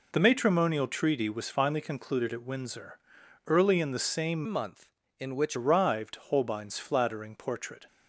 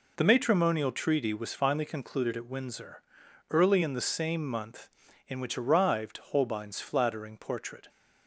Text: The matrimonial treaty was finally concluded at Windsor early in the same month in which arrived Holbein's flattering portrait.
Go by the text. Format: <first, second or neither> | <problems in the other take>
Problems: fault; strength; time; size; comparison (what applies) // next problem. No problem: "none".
second | pauses between "Windsor" and "early"; noticeable; at 2.9 s; 0.48 s long; noticeable in the second // changes voice from "month" to "which"; from 4.4 to 5.5 s; 1.1 s long